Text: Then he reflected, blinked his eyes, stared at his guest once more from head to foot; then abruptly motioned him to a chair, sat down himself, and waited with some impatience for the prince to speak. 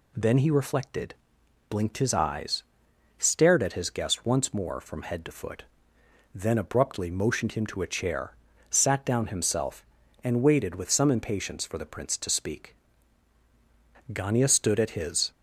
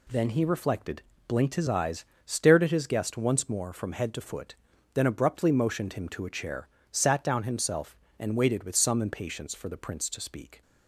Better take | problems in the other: second | goes on to say "Gania stood at his"; noticeable; from 14.1 s on; 1.2 s long

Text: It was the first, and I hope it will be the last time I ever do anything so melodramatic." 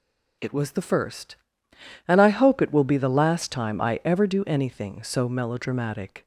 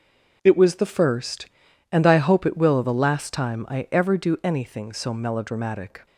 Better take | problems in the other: first | starts louder than the rest; noticeable; until 1.4 s; 6 dB // skips "be"; at 2.8 s

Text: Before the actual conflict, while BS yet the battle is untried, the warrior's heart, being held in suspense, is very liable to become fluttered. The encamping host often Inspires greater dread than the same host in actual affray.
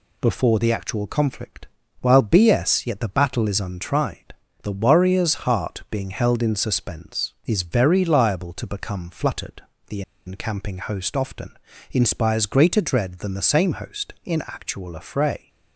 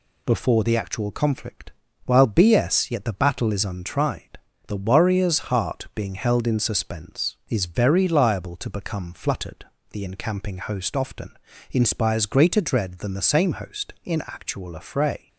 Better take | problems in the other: second | pauses between "The" and "encamping"; slight; at 10.0 s; 0.24 s long // pauses between "often" and "Inspires"; slight; at 11.5 s; 0.34 s long; slight in the second

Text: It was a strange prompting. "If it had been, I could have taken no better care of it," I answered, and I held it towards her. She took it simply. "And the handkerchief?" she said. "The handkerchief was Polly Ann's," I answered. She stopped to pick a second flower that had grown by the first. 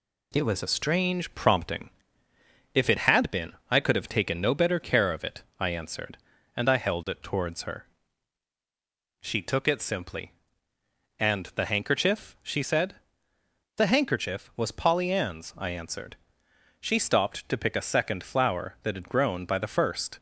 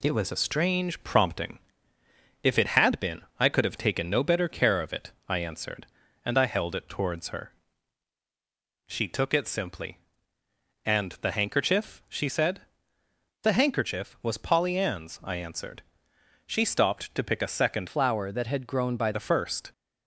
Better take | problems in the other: first | changes voice from "flower" to "by"; from 17.8 to 19.1 s; 1.3 s long

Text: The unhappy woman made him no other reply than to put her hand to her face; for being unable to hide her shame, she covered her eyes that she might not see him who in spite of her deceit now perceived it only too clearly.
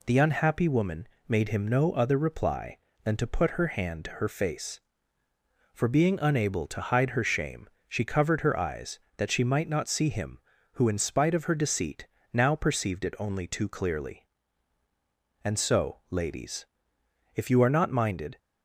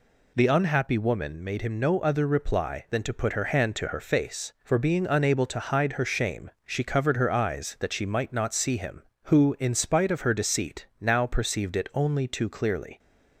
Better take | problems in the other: second | pauses between "woman" and "made"; slight; at 1.0 s; 0.22 s long // pauses between "deceit" and "now"; slight; at 12.0 s; 0.26 s long // goes on to say "And so ladies if you are not minded"; strong; from 15.4 s on; 2.9 s long

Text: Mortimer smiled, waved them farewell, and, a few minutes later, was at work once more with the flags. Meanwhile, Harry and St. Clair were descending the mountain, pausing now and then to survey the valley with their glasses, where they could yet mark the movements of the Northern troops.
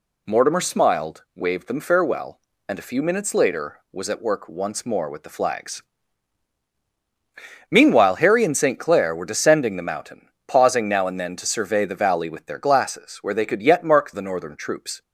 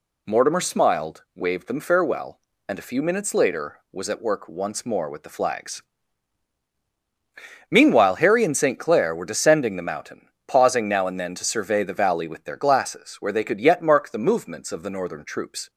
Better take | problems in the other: second | skips "the movements of"; at 14.1 s

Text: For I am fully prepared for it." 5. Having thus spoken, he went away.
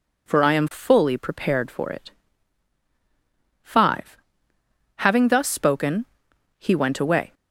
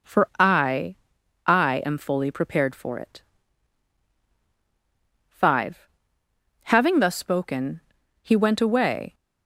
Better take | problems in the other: first | says "I" twice; at 1.4 s

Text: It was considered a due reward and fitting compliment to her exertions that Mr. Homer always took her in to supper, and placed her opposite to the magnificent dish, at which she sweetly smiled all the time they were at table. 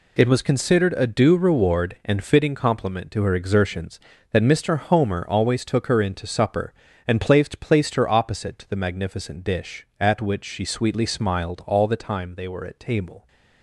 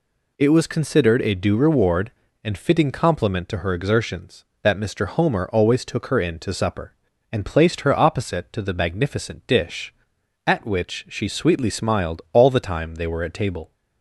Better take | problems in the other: second | says "placed" twice; at 7.5 s

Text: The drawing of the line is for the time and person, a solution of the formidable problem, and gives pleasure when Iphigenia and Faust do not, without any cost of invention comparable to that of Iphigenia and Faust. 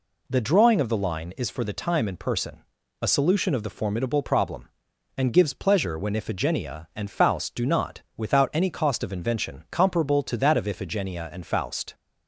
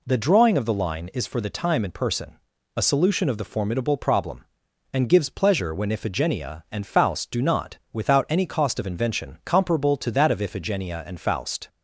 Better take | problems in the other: neither | none

